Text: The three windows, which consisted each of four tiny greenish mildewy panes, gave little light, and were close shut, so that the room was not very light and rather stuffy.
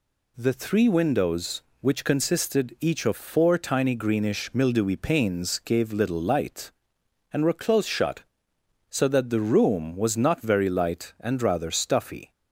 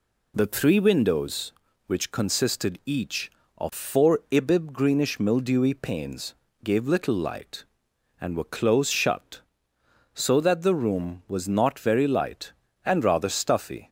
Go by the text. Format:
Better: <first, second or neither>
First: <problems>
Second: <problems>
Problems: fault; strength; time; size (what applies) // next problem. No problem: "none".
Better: first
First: none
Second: says "ibib" for "tiny"; at 4.2 s